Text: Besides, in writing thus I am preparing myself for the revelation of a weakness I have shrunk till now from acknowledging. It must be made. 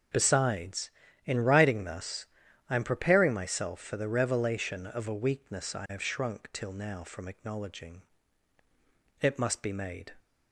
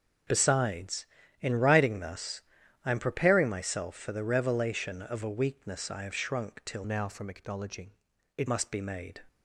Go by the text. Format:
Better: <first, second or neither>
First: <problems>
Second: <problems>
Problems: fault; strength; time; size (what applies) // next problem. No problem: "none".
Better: first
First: pauses between "thus" and "I"; at 2.2 s; 0.42 s long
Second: pauses between "thus" and "I"; at 2.4 s; 0.42 s long // changes voice from "now" to "It"; from 6.8 to 8.4 s; 1.6 s long